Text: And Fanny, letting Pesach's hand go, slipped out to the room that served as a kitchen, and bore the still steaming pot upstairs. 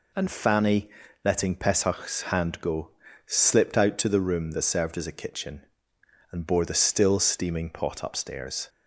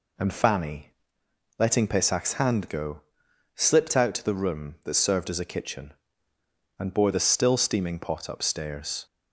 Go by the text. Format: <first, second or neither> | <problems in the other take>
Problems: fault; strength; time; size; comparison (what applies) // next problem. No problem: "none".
neither | none